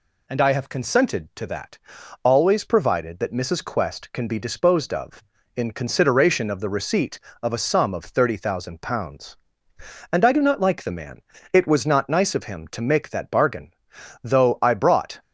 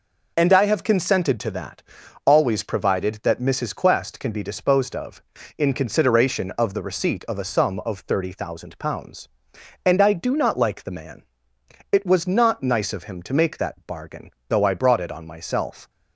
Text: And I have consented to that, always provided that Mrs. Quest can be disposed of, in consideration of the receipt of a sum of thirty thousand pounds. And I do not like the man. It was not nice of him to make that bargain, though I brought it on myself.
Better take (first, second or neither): second